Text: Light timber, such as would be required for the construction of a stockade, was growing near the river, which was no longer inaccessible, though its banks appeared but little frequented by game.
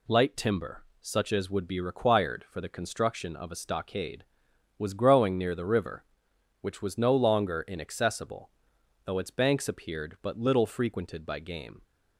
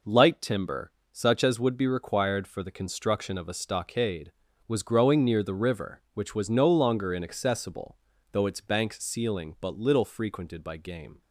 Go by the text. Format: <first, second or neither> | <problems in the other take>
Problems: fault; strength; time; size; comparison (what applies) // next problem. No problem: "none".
first | says "ceiling" for "appeared"; at 9.0 s